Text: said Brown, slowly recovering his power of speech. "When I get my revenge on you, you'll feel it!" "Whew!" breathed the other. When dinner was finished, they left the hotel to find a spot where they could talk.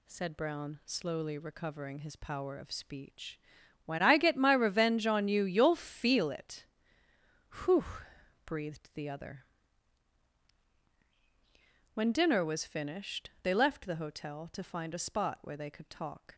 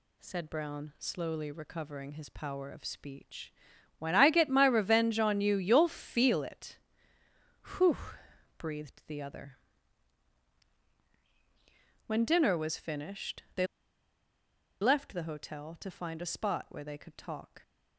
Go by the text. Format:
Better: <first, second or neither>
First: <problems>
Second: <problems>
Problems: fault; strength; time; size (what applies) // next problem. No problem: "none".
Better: first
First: none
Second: pauses between "they" and "left"; at 13.6 s; 1.1 s long